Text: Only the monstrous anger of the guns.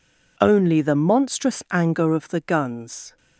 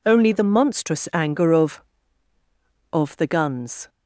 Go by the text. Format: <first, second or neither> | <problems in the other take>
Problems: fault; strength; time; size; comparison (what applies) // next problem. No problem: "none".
first | says "of" twice; at 2.9 s